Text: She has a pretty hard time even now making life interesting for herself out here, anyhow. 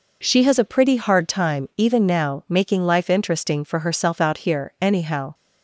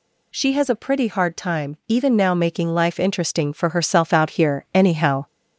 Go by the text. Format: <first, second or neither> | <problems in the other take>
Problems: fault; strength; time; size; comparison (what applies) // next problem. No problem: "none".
first | gets louder; slight; throughout; 3 dB